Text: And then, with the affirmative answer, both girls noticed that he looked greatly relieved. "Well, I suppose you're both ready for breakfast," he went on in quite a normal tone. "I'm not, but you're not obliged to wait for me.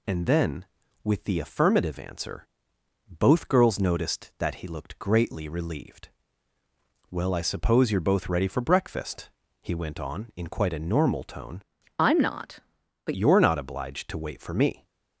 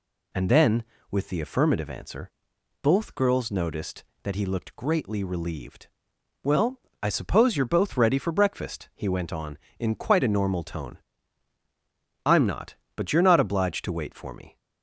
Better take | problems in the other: second | changes voice from "I'm" to "but"; from 11.9 to 13.1 s; 1.2 s long

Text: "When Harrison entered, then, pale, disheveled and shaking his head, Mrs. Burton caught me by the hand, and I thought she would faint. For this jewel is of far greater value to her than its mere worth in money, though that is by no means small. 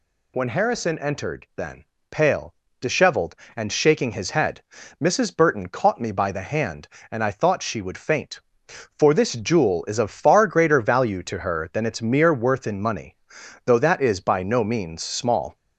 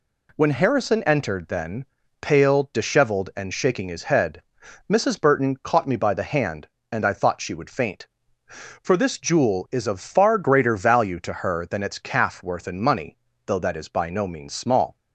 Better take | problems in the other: first | says "calf" for "mere"; at 11.9 s

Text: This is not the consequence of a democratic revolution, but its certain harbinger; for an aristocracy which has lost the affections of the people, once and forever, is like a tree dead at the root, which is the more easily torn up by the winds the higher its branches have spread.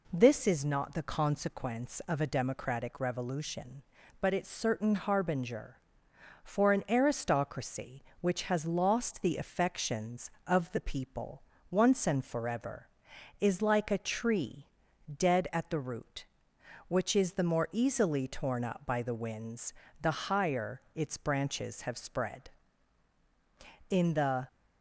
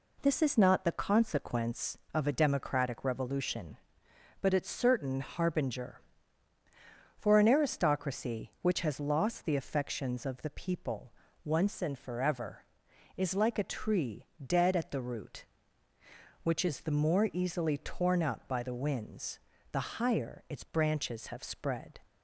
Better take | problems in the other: second | pauses between "tree" and "dead"; at 14.6 s; 0.44 s long; slight in the second // pauses between "winds" and "the"; slight; at 19.7 s; 0.28 s long; slight in the second // goes on to say "In the"; from 23.8 s on; 0.58 s long

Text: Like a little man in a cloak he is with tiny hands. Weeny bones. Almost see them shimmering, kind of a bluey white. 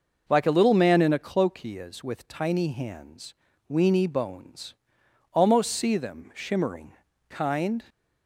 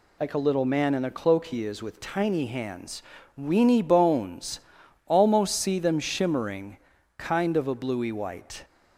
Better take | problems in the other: second | stops before "of a bluey white"; at 7.8 s

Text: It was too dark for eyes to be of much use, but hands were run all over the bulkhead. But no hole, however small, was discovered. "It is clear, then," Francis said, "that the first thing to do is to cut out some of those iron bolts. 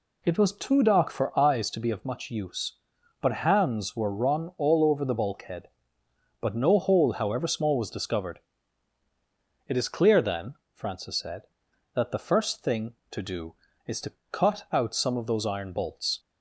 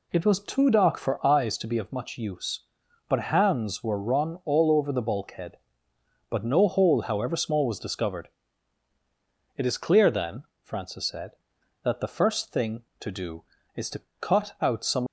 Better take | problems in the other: first | pauses between "to" and "cut"; slight; at 14.0 s; 0.18 s long; slight in the first // stops before "of those iron bolts"; at 15.0 s

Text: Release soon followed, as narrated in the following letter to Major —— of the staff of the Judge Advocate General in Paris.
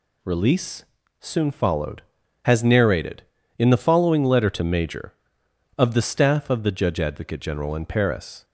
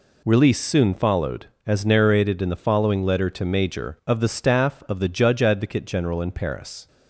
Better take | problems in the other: second | pauses between "Release" and "soon"; slight; at 0.8 s; 0.34 s long // says "has" for "as"; at 2.4 s

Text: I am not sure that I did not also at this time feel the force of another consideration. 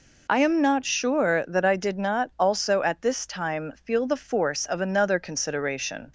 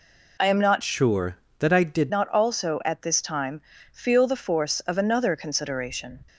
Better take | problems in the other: first | changes voice from "sure" to "did"; from 0.8 to 2.1 s; 1.3 s long // pauses between "time" and "feel"; slight; at 3.5 s; 0.32 s long

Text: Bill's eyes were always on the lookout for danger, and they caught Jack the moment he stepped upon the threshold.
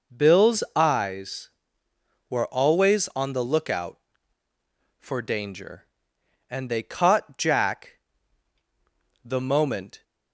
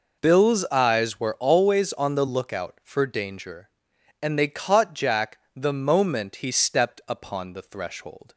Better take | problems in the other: second | pauses between "Jack" and "the"; at 7.9 s; 1.2 s long; slight in the second // stops before "he stepped upon the threshold"; at 10.0 s

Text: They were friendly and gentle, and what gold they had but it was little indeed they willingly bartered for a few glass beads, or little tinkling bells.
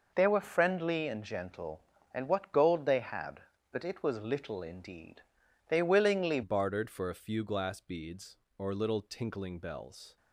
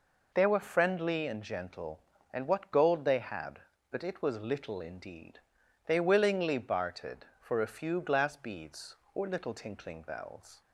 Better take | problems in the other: second | pauses between "indeed" and "they"; noticeable; at 5.2 s; 0.48 s long; noticeable in the second // changes voice at "bartered"; from 6.4 s on; 3.7 s long

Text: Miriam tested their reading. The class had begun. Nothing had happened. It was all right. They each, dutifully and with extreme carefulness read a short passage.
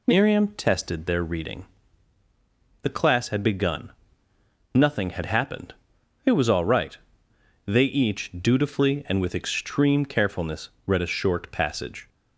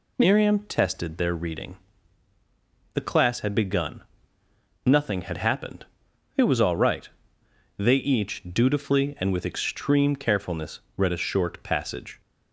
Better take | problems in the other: neither | pauses between "carefulness" and "read"; slight; the same in both

